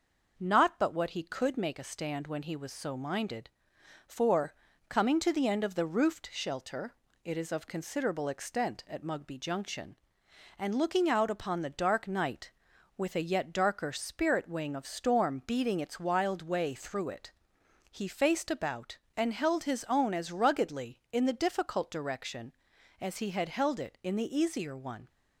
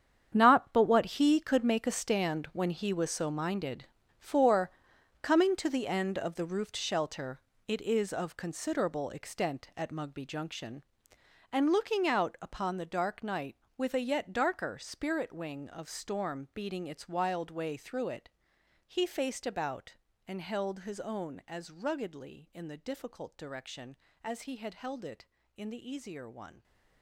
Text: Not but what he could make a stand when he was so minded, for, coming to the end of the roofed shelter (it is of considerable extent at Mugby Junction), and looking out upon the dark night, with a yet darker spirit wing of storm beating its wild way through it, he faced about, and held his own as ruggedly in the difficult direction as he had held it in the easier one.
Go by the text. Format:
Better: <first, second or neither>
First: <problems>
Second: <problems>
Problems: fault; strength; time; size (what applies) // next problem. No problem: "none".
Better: first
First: none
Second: gets quieter; strong; throughout; 13.5 dB